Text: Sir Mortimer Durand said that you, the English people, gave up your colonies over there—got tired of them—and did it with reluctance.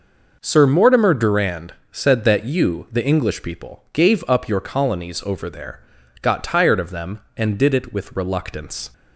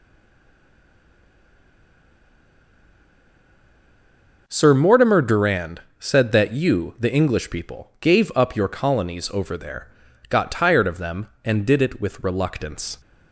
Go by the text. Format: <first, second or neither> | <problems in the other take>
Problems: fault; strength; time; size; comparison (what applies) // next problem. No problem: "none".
first | stays silent before the first word; strong; until 4.4 s; 4.4 s long // pauses between "Durand" and "said"; slight; at 5.8 s; 0.18 s long; slight in the first